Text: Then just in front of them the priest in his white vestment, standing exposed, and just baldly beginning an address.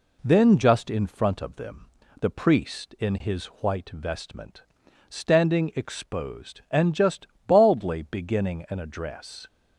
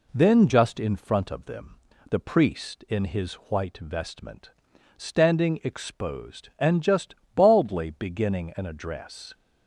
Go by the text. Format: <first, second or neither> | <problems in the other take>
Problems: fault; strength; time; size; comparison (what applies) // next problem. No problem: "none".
neither | pauses between "them" and "the"; slight; the same in both // pauses between "his" and "white"; slight; the same in both // pauses between "just" and "baldly"; slight; the same in both